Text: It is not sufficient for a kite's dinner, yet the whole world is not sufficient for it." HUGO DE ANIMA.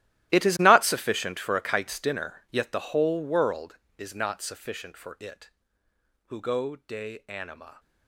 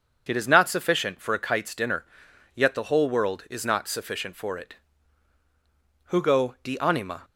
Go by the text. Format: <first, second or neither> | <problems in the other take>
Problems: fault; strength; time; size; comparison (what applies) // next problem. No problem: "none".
second | gets quieter; strong; throughout; 16 dB // starts louder than the rest; strong; until 1.3 s; 14.5 dB; also in the second